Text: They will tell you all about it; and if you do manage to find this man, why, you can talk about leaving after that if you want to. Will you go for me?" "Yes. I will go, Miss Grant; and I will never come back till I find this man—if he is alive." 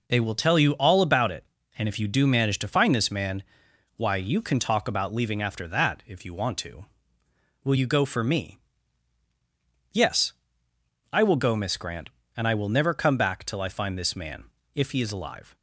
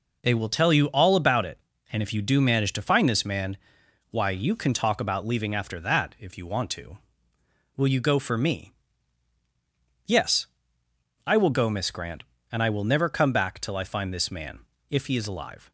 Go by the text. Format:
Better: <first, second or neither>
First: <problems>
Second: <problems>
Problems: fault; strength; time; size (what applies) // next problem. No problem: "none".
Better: neither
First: none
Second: none